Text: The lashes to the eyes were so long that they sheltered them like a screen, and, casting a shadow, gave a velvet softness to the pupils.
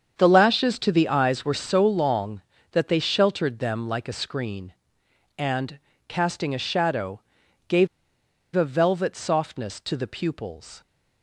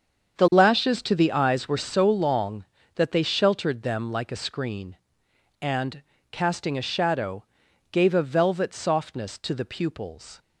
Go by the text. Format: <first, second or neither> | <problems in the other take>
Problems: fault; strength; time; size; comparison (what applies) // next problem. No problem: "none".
second | starts louder than the rest; strong; until 1.1 s; 7.5 dB; strong in the second // pauses between "gave" and "a"; noticeable; at 7.8 s; 0.67 s long